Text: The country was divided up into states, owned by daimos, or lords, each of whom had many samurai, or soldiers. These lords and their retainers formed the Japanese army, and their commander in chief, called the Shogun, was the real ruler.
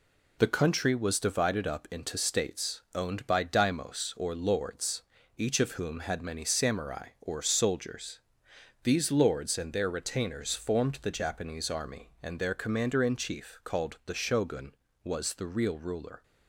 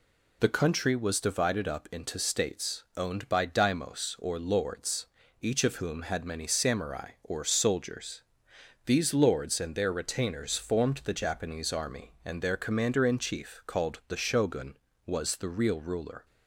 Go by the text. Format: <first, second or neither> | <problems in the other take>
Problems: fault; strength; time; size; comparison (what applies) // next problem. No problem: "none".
second | gets quieter; noticeable; throughout; 5 dB